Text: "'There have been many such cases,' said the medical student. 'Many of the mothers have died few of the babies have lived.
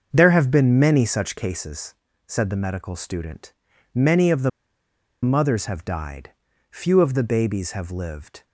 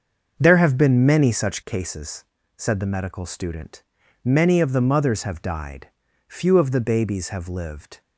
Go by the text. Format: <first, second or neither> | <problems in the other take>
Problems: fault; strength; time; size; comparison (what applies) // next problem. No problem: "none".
second | starts louder than the rest; until 1.1 s; 6.5 dB; also in the second // pauses between "the" and "mothers"; noticeable; at 4.4 s; 0.73 s long // pauses between "died" and "few"; at 6.2 s; 0.40 s long; also in the second